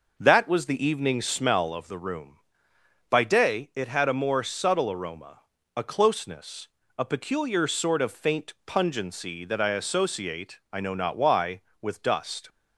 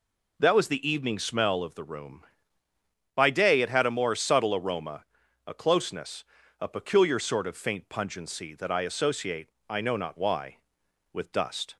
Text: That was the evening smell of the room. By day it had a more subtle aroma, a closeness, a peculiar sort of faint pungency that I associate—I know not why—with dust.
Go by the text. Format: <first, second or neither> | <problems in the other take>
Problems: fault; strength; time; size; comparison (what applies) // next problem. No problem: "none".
second | starts louder than the rest; noticeable; until 1.5 s; 5.5 dB